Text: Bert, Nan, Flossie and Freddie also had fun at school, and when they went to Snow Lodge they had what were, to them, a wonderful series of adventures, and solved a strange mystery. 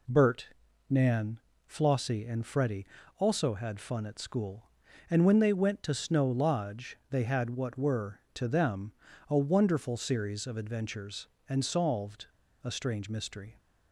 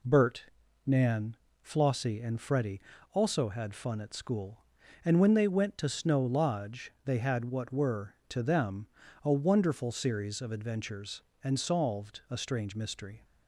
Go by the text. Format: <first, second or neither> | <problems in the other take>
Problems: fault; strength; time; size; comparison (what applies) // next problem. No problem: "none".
second | pauses between "Freddie" and "also"; slight; at 2.8 s; 0.32 s long; slight in the second // pauses between "solved" and "a"; at 12.2 s; 0.36 s long